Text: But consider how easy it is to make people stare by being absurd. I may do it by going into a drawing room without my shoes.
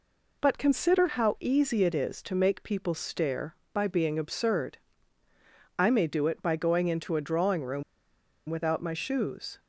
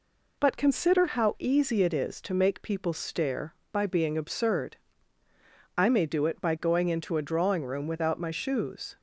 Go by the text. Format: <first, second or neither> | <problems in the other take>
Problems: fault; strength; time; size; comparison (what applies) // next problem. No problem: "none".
second | pauses between "room" and "without"; noticeable; at 7.8 s; 0.66 s long